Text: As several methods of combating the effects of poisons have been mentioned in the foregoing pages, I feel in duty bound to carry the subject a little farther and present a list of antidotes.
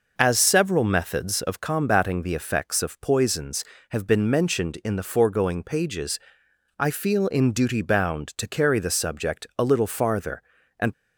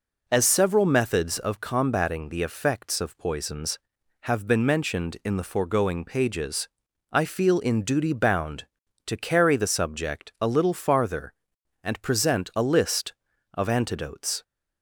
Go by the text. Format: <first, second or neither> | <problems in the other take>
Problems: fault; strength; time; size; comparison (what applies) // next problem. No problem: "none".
second | stops before "present a list of antidotes"; at 10.9 s